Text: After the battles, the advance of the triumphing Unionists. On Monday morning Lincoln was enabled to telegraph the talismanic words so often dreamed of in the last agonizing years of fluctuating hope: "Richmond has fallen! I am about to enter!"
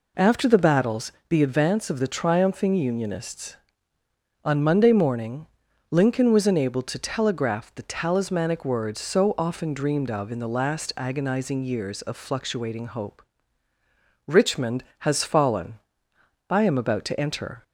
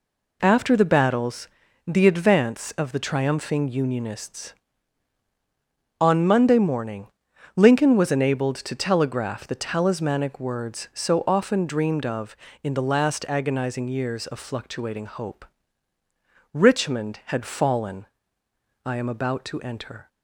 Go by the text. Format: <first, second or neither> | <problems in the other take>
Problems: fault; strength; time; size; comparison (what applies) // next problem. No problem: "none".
first | pauses between "morning" and "Lincoln"; noticeable; at 7.0 s; 0.48 s long; also in the first // says "had" for "has"; at 17.2 s